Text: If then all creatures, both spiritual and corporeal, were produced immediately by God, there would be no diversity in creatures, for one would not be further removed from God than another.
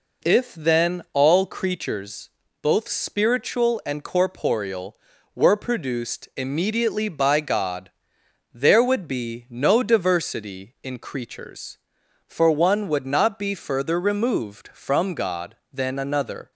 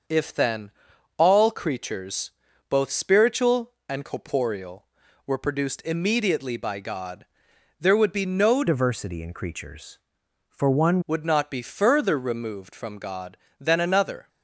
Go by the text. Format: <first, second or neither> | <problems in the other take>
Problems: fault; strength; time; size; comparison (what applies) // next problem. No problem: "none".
first | starts louder than the rest; until 1.5 s; 6.5 dB // pauses between "then" and "all"; noticeable; at 0.7 s; 0.46 s long // changes voice from "diversity" to "one"; from 8.6 to 10.9 s; 2.3 s long